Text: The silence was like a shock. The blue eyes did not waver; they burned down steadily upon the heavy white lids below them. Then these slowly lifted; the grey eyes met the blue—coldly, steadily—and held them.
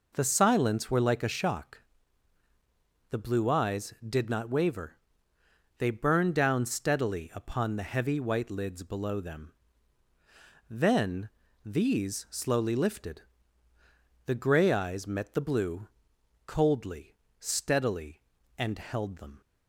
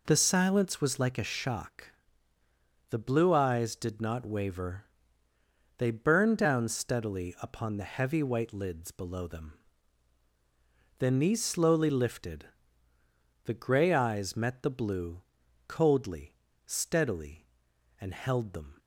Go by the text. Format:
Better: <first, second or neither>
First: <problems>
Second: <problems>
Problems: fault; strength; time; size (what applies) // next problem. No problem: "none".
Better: second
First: says "were" for "was"; at 0.9 s // pauses between "Then" and "these"; slight; at 11.3 s; 0.34 s long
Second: none